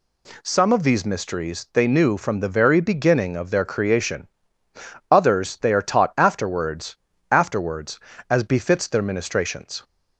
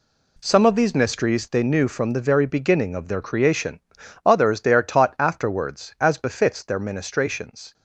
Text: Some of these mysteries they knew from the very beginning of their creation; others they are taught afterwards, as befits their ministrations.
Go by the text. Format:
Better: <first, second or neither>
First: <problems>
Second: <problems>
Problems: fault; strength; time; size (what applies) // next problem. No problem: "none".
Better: second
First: says "afterwards" twice; at 7.3 s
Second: none